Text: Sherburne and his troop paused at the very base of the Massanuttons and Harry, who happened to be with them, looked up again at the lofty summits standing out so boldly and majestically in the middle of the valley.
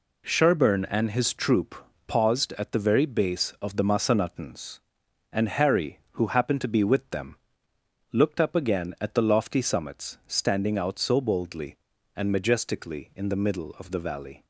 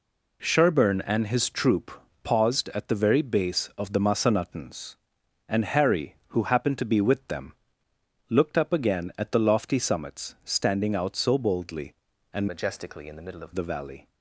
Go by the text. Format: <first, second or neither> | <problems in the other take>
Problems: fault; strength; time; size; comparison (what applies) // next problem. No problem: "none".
first | pauses between "troop" and "paused"; slight; at 1.9 s; 0.32 s long; slight in the first // changes voice from "majestically" to "of"; from 12.4 to 13.5 s; 1.1 s long